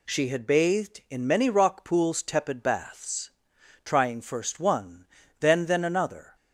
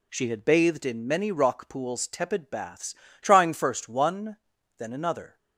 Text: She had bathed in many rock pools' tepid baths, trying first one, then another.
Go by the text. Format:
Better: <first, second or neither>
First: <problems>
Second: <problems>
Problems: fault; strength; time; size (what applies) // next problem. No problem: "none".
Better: second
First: says "then" twice; at 5.6 s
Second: none